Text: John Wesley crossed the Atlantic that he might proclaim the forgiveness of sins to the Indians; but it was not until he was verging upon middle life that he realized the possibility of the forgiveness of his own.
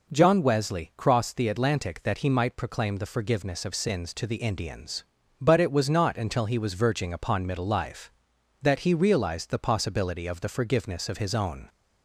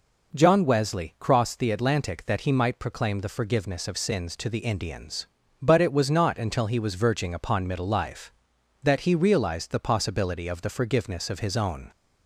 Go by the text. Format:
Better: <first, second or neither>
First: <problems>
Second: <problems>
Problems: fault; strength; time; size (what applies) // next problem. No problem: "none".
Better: neither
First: none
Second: none